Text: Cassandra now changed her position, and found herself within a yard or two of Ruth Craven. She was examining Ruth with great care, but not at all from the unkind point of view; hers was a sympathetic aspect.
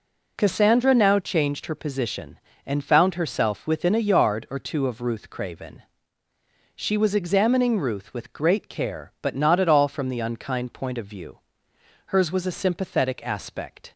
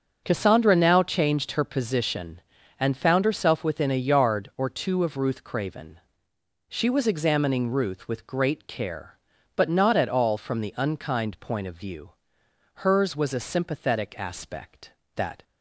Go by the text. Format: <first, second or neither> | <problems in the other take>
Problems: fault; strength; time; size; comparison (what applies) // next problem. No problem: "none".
first | starts louder than the rest; until 1.2 s; 6.5 dB // goes on to say "That"; slight; from 15.1 s on; 0.28 s long